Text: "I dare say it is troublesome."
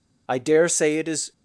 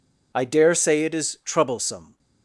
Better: second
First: stops before "troublesome"; at 1.3 s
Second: none

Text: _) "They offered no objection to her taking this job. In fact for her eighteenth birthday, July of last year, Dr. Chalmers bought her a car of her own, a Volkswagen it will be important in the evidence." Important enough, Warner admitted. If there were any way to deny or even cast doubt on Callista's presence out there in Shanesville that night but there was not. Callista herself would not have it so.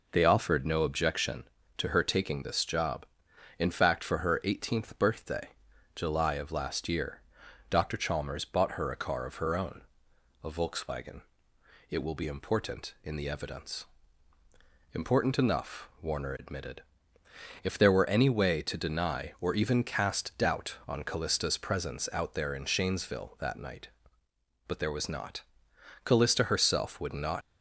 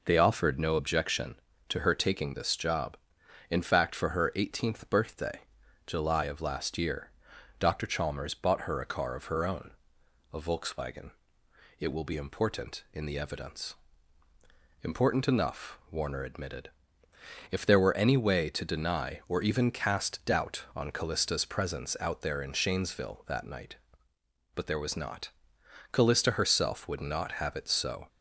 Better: second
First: pauses between "Volkswagen" and "it"; noticeable; at 11.2 s; 0.70 s long // stops before "have it so"; at 27.4 s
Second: pauses between "Volkswagen" and "it"; noticeable; at 11.0 s; 0.70 s long

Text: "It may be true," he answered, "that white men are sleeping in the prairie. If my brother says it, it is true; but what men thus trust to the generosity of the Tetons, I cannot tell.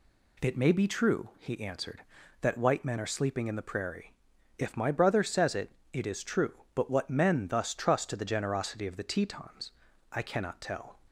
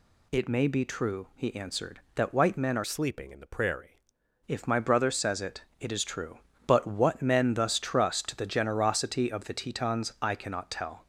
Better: first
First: none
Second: changes voice from "sleeping" to "prairie"; from 2.8 to 4.0 s; 1.2 s long

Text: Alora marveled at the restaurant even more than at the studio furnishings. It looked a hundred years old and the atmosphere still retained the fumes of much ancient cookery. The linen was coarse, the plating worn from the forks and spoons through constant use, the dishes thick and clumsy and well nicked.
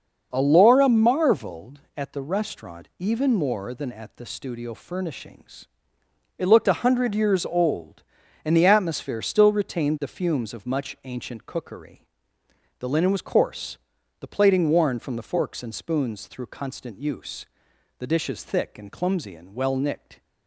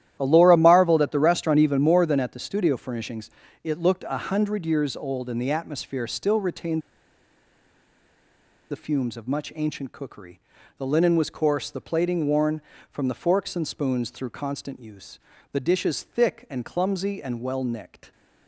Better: first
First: starts louder than the rest; until 1.3 s; 6 dB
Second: starts louder than the rest; strong; until 1.2 s; 12 dB // pauses between "retained" and "the"; strong; at 6.8 s; 1.9 s long

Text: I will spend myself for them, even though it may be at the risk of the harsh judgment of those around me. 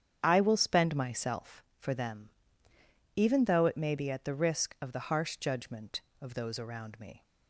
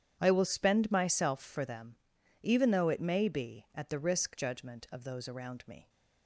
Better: first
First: starts louder than the rest; strong; until 1.2 s; 8.5 dB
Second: starts louder than the rest; strong; until 1.2 s; 9 dB // skips "of the harsh"; at 4.3 s

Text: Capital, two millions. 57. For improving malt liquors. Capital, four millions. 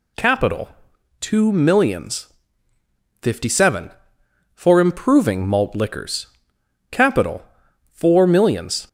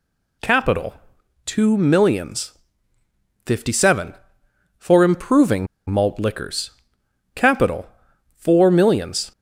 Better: first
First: none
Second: pauses between "improving" and "malt"; slight; at 5.6 s; 0.23 s long

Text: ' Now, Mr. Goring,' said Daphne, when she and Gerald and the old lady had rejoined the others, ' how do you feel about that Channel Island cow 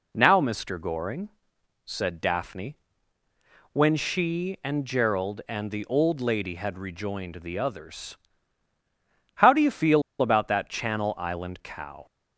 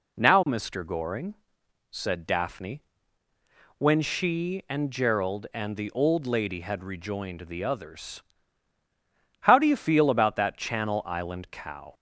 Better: second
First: pauses between "feel" and "about"; slight; at 10.0 s; 0.19 s long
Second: none

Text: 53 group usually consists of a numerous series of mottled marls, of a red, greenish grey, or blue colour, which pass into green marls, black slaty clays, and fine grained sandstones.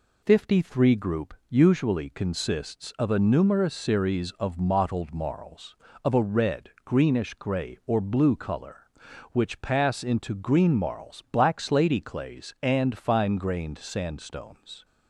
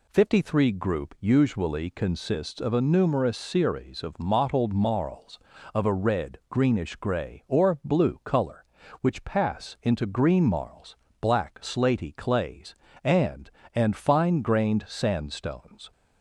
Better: first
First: none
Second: says "and" twice; at 13.7 s

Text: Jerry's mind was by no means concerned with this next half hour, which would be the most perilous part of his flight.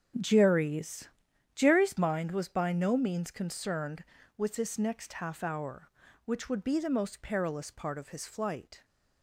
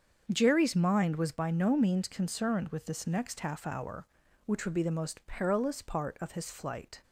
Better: second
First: starts louder than the rest; strong; until 1.6 s; 8 dB // says "Jerry's" twice; at 1.5 s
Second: starts louder than the rest; until 1.3 s; 7 dB

